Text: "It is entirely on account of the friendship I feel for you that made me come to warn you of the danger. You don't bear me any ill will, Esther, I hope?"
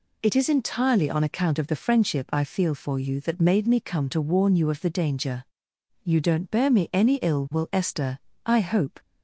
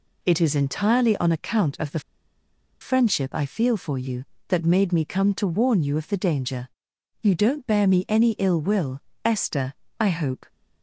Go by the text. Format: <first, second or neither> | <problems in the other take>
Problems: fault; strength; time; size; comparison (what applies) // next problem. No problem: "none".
first | pauses between "the" and "friendship"; noticeable; at 1.9 s; 0.81 s long